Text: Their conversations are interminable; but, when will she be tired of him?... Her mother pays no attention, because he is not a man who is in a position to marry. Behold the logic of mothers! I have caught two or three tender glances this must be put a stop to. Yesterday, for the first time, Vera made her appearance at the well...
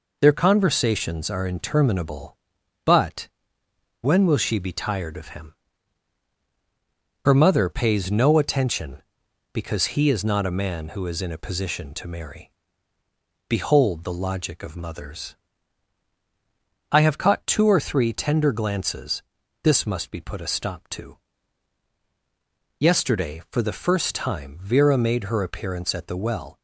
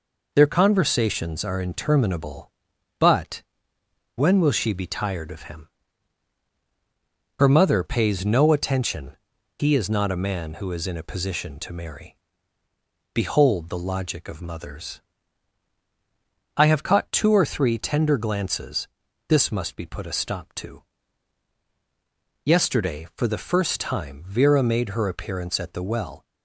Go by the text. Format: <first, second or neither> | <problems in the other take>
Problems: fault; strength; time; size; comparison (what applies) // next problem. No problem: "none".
first | skips "because"; at 9.3 s // pauses between "glances" and "this"; at 18.8 s; 0.42 s long; also in the first